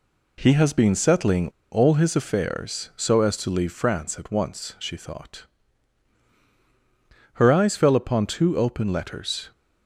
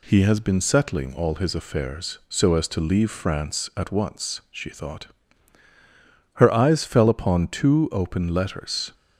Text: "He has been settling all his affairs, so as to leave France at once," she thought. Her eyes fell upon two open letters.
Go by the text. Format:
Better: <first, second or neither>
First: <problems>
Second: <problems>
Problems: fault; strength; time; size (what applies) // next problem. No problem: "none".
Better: second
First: pauses between "settling" and "all"; slight; at 1.4 s; 0.22 s long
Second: none